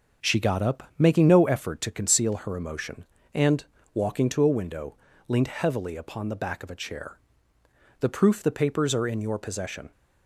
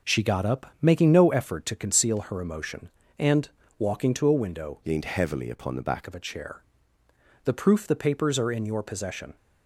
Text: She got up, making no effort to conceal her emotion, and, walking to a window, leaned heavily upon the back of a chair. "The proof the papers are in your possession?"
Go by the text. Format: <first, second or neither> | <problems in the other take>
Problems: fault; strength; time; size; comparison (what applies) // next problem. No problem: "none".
first | starts louder than the rest; until 1.2 s; 6.5 dB; also in the first // changes voice from "leaned" to "back"; from 4.8 to 6.0 s; 1.2 s long